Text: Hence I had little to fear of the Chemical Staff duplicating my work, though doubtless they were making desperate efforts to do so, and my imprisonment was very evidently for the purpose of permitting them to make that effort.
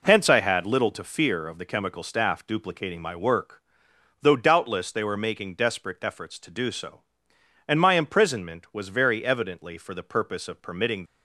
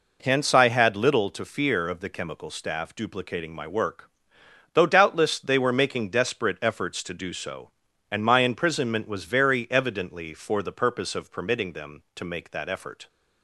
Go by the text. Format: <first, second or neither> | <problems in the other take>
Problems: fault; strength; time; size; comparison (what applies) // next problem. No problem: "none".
second | stops before "them to make that effort"; at 11.0 s